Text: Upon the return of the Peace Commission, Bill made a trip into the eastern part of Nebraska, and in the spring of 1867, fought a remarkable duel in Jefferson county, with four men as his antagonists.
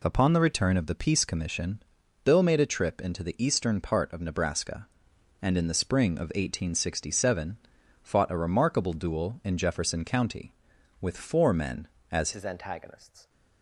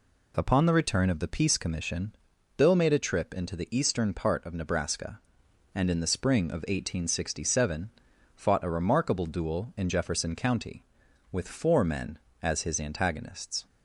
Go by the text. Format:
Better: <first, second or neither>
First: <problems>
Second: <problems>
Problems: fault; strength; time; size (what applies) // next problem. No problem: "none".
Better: second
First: changes voice at "his"; from 12.3 s on; 0.9 s long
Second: none